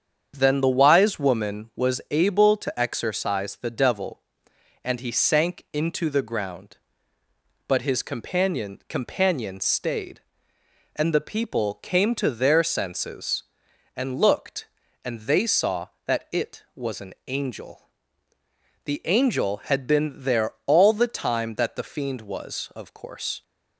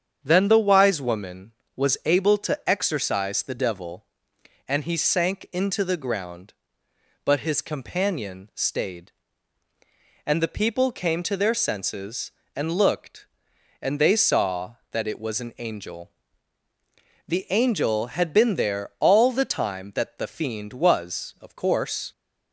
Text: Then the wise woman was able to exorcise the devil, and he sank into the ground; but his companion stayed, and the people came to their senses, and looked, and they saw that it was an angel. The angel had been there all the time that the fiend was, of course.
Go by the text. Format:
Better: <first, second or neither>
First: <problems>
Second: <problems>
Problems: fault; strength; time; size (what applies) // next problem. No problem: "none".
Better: second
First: starts louder than the rest; strong; until 1.3 s; 7.5 dB // says "companion" twice; at 8.8 s // pauses between "an" and "angel"; slight; at 17.1 s; 0.16 s long // pauses between "there" and "all"; slight; at 20.5 s; 0.16 s long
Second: starts louder than the rest; strong; until 1.2 s; 7.5 dB